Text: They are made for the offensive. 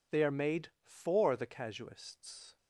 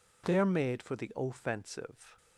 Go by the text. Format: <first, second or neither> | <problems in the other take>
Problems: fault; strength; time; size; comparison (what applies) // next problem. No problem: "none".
second | says "casuists" for "offensive"; at 1.4 s